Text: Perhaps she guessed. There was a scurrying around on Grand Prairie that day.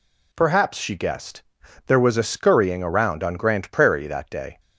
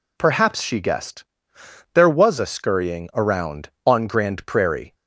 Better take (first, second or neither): first